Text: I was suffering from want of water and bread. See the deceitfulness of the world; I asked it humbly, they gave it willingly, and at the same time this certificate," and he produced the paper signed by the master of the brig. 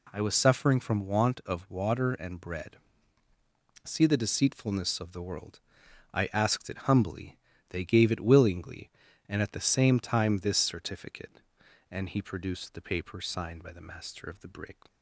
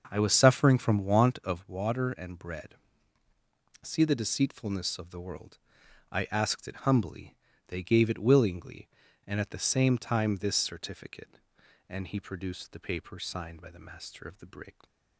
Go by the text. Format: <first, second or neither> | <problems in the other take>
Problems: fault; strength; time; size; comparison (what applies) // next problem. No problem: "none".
first | starts louder than the rest; until 1.7 s; 6.5 dB